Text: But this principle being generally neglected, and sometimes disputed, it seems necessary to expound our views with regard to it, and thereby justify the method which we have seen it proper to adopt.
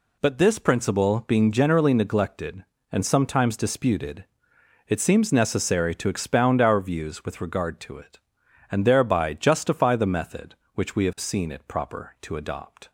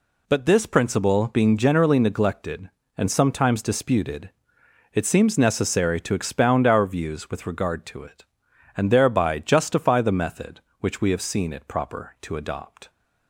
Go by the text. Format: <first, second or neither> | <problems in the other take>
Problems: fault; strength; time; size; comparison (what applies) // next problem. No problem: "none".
neither | none